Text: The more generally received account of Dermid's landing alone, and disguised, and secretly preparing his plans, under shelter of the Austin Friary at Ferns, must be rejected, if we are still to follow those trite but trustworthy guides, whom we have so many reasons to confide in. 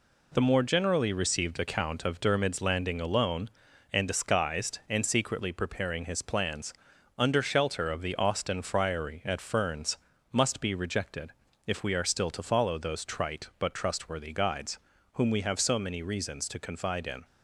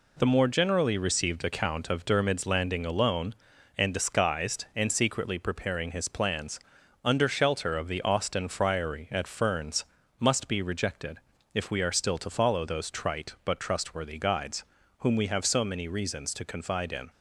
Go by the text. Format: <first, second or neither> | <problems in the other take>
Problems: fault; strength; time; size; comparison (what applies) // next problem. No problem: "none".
neither | none